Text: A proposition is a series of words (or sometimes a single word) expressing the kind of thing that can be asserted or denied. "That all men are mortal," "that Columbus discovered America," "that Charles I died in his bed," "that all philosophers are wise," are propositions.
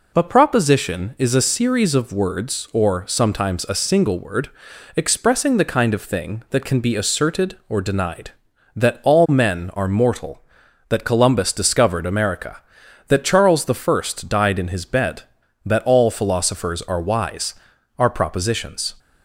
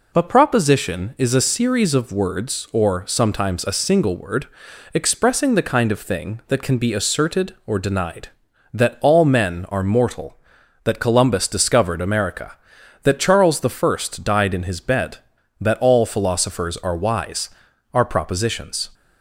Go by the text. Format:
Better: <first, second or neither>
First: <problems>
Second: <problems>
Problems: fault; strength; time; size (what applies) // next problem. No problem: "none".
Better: neither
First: none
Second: none